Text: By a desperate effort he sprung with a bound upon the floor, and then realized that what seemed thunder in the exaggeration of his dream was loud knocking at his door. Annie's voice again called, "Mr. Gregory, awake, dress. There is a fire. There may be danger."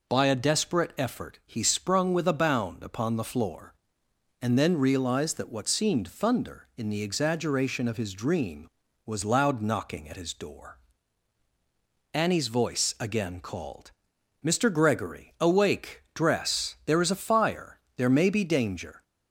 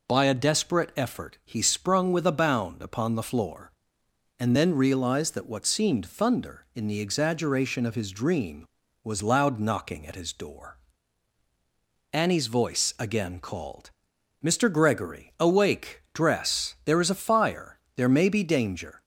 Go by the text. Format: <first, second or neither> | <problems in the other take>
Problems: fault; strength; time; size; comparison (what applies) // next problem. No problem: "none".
neither | none